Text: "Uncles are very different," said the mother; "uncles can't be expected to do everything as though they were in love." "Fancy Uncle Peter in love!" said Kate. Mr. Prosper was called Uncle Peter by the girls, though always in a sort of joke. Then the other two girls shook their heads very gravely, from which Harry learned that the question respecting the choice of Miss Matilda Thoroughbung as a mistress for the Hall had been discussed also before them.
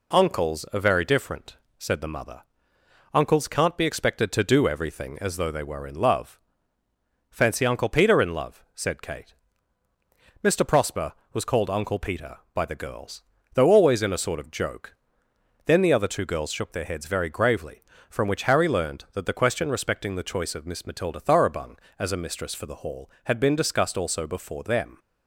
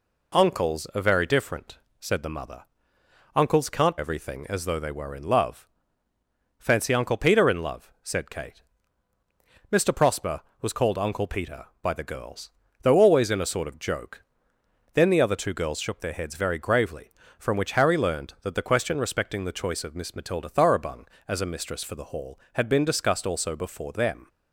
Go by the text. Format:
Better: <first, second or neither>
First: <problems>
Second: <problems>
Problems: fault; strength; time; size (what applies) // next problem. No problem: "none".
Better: first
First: none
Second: skips "be expected to do"; at 3.9 s